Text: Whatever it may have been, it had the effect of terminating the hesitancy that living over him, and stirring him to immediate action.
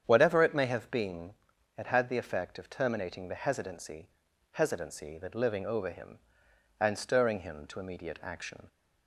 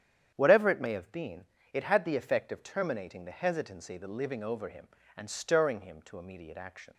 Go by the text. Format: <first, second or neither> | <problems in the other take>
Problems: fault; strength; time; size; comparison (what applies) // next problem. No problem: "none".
second | starts louder than the rest; strong; until 1.0 s; 8.5 dB; strong in the second // says "hesitancy" twice; at 4.5 s